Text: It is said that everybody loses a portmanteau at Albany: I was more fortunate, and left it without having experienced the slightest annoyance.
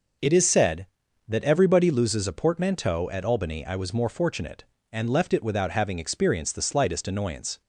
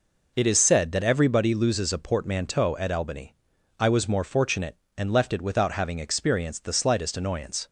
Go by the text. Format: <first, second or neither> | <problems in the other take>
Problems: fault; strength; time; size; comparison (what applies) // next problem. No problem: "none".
neither | none